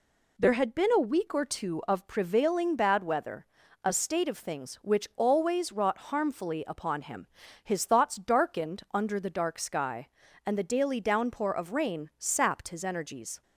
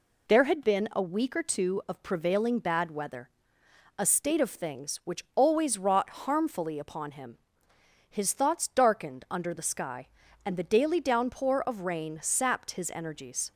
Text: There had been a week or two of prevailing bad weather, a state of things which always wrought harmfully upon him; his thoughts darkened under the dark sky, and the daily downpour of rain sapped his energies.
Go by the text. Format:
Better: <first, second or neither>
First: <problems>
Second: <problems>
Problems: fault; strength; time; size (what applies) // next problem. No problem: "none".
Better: first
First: none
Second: pauses between "wrought" and "harmfully"; slight; at 6.1 s; 0.16 s long // skips "dark"; at 9.6 s